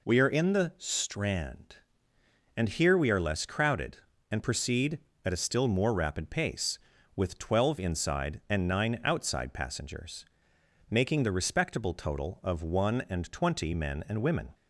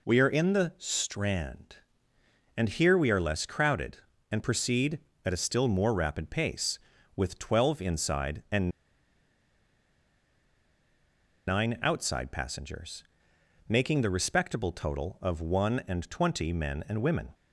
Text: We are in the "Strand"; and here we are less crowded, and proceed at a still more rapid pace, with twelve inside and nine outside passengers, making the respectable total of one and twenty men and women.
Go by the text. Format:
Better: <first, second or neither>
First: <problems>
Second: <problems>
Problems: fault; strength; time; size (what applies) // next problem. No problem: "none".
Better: first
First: none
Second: pauses between "and" and "nine"; strong; at 8.6 s; 2.7 s long